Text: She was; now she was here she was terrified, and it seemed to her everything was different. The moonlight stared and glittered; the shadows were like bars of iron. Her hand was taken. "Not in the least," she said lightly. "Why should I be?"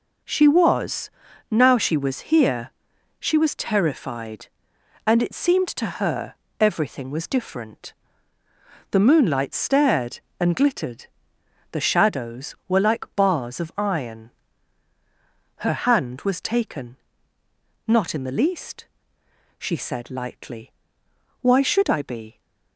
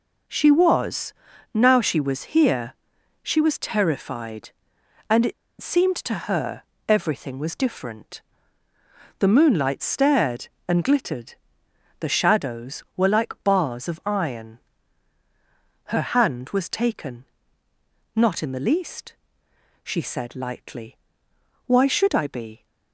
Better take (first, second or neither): first